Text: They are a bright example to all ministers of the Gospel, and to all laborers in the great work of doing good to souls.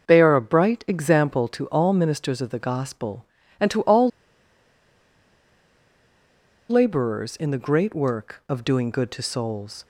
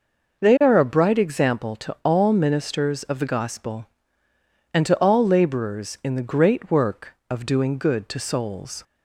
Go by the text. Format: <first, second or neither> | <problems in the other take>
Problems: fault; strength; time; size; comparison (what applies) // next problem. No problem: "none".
second | starts louder than the rest; until 1.1 s; 6 dB // pauses between "all" and "laborers"; strong; at 4.0 s; 2.6 s long